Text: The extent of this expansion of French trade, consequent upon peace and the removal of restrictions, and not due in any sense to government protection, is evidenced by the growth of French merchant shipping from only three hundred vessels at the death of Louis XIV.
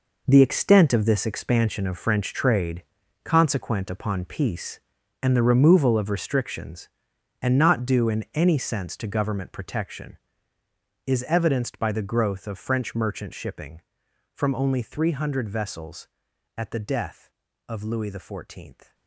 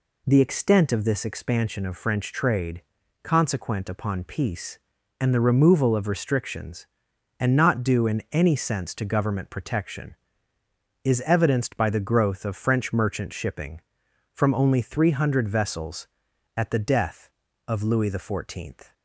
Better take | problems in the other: second | gets quieter; strong; throughout; 12.5 dB

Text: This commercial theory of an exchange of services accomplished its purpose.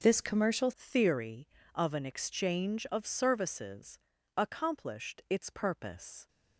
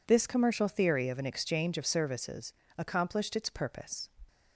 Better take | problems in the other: second | starts louder than the rest; until 1.0 s; 6 dB // changes voice at "theory"; from 0.7 s on; 5.5 s long // pauses between "services" and "accomplished"; at 3.9 s; 0.38 s long; slight in the second

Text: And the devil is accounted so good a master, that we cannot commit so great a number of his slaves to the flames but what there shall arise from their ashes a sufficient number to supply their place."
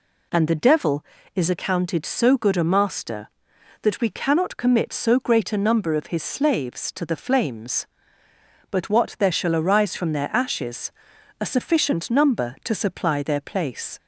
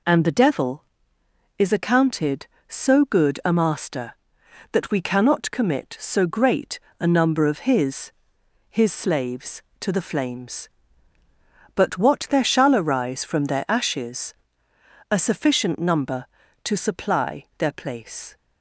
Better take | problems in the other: first | pauses between "great" and "a"; slight; at 6.8 s; 0.18 s long // says "his" twice; at 8.6 s // pauses between "ashes" and "a"; noticeable; at 14.3 s; 0.78 s long; noticeable in the first // pauses between "supply" and "their"; slight; at 17.4 s; 0.16 s long

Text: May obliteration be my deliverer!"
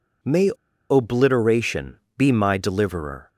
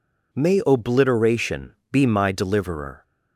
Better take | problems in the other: second | pauses between "May" and "obliteration"; at 0.5 s; 0.38 s long // pauses between "obliteration" and "be"; slight; at 1.9 s; 0.20 s long; slight in the second

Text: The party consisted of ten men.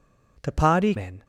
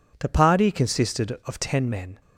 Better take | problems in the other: second | skips "consisted of ten"; at 0.9 s

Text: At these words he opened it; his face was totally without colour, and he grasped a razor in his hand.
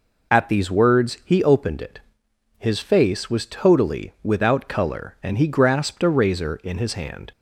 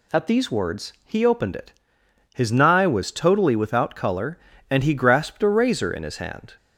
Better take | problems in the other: first | says "nigh" for "face"; at 2.5 s

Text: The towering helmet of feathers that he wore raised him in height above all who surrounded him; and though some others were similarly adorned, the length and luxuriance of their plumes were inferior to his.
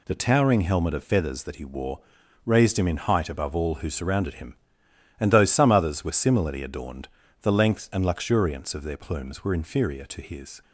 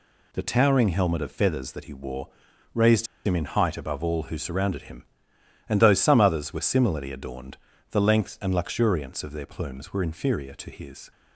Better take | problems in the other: first | pauses between "wore" and "raised"; at 2.2 s; 0.44 s long; also in the first // pauses between "raised" and "him"; slight; at 3.0 s; 0.20 s long

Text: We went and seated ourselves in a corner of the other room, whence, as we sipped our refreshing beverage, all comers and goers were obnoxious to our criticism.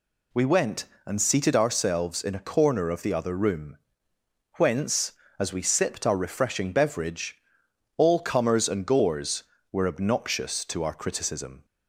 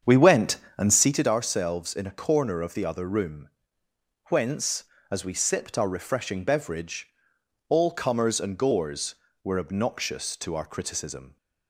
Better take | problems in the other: first | starts louder than the rest; strong; until 1.1 s; 7.5 dB

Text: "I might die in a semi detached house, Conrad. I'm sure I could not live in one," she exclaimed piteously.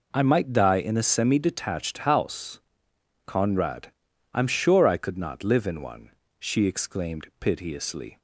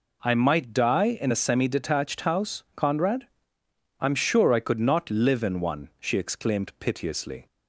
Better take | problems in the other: neither | none

